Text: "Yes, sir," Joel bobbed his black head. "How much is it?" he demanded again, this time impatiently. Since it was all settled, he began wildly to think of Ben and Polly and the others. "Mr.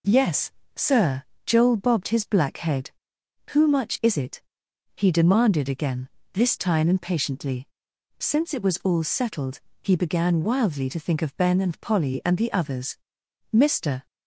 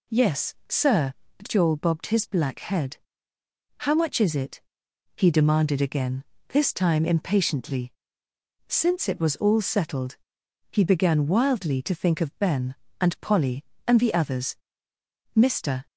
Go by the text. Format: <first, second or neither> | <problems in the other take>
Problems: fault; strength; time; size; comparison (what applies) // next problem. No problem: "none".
second | says "Who" for "How"; at 3.4 s